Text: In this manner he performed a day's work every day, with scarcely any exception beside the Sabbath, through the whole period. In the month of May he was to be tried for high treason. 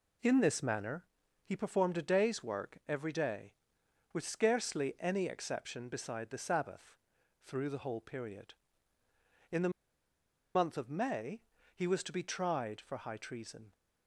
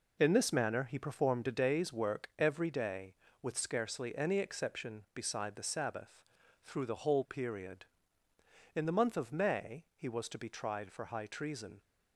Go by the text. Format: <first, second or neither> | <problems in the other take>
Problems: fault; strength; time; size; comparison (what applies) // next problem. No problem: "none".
second | pauses between "manner" and "he"; at 1.0 s; 0.40 s long // pauses between "the" and "month"; noticeable; at 9.6 s; 0.85 s long // pauses between "May" and "he"; slight; at 11.4 s; 0.34 s long